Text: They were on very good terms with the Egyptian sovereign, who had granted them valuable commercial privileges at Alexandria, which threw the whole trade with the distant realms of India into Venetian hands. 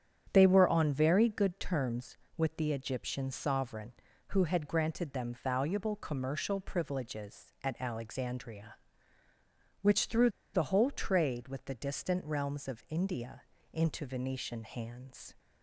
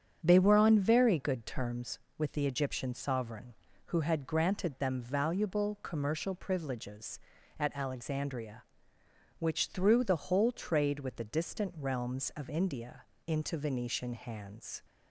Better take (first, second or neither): second